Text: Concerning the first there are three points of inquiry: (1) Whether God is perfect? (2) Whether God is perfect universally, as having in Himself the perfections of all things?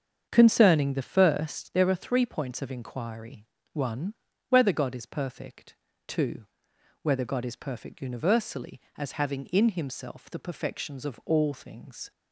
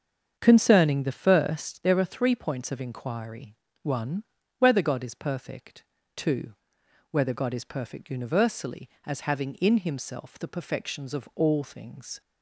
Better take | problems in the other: neither | starts louder than the rest; strong; the same in both

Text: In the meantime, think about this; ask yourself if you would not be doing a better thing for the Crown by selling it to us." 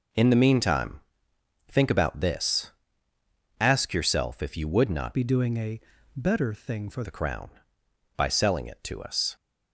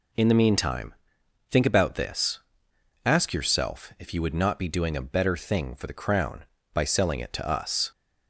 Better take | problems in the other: second | changes voice from "be" to "for"; from 5.1 to 7.0 s; 1.9 s long // pauses between "a" and "better"; slight; at 5.7 s; 0.34 s long

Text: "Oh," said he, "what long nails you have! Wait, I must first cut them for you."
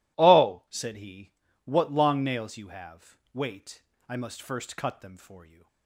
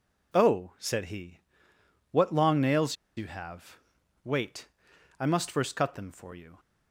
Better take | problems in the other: first | pauses between "nails" and "you"; slight; at 2.9 s; 0.22 s long

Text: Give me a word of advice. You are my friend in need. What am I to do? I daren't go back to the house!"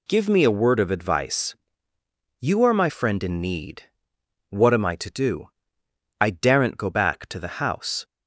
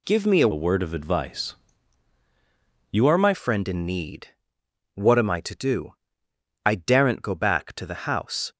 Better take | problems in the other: first | changes voice from "word" to "my"; from 0.5 to 3.3 s; 2.8 s long

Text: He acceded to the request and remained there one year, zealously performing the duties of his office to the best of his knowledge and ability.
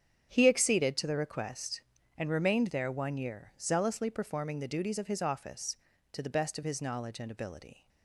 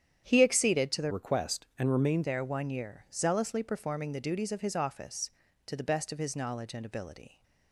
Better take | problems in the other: first | starts louder than the rest; strong; until 1.2 s; 9 dB; strong in the first // changes voice from "request" to "remained"; from 1.0 to 2.2 s; 1.2 s long

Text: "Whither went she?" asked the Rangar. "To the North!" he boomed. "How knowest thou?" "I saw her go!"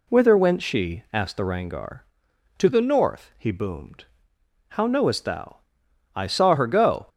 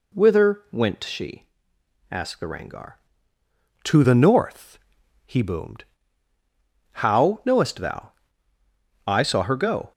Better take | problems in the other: neither | none

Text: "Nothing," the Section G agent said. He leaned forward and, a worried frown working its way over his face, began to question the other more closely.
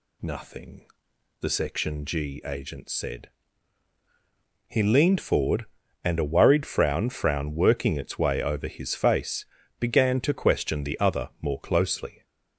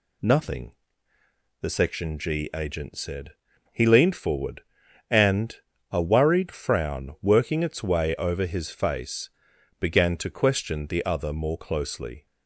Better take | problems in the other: second | says "frown" twice; at 7.0 s

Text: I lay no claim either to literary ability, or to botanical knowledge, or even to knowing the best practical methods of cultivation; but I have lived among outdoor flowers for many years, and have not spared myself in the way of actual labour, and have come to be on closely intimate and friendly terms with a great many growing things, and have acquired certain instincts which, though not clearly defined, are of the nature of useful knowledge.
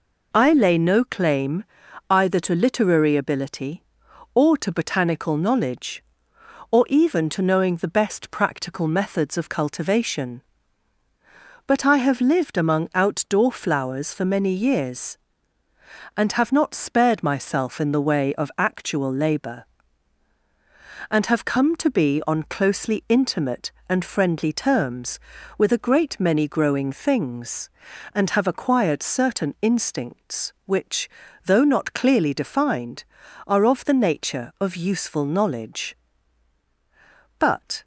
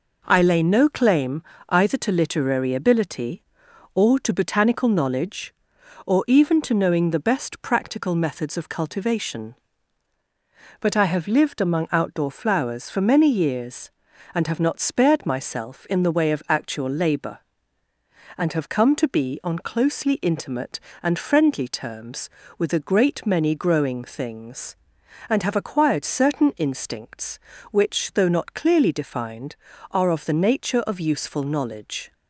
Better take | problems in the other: second | pauses between "claim" and "either"; at 1.6 s; 0.44 s long; slight in the second // goes on to say "But"; slight; from 37.3 s on; 0.44 s long

